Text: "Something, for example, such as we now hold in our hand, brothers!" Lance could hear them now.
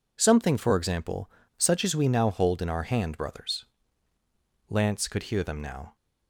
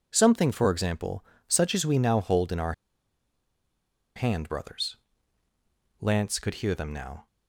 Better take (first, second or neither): first